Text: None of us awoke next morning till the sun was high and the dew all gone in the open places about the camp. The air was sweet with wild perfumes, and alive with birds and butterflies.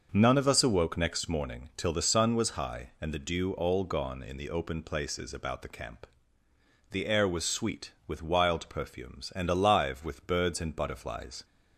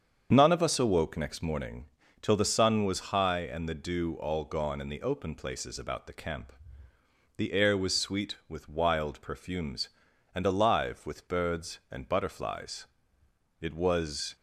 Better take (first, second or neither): first